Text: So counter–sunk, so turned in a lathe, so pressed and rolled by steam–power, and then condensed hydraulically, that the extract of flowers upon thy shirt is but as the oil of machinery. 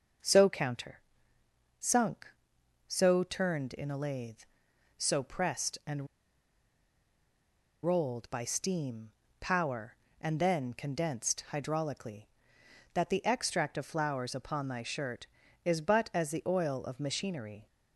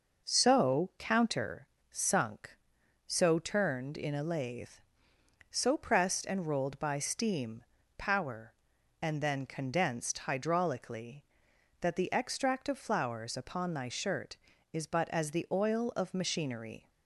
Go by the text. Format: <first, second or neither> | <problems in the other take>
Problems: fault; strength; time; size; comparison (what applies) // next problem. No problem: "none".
second | starts louder than the rest; until 2.0 s; 6.5 dB // pauses between "and" and "rolled"; strong; at 6.0 s; 1.7 s long